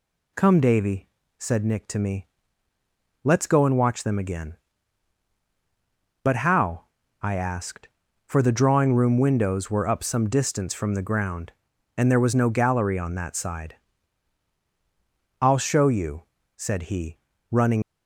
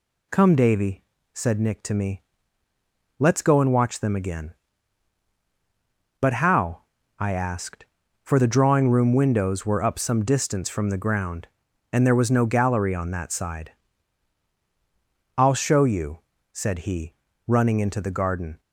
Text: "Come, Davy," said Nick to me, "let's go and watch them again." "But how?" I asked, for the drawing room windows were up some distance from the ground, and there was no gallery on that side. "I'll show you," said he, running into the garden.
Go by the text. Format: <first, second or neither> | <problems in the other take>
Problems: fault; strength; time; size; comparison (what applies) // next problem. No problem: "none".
second | stops before "into the garden"; at 17.8 s